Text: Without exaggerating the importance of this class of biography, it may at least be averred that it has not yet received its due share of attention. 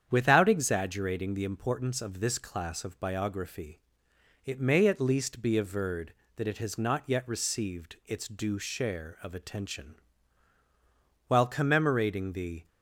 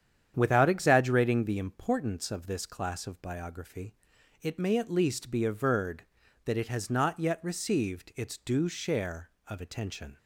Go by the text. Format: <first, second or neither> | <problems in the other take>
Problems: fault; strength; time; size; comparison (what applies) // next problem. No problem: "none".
second | starts louder than the rest; strong; until 1.1 s; 8.5 dB; strong in the second // goes on to say "While commemorating the"; from 11.2 s on; 1.4 s long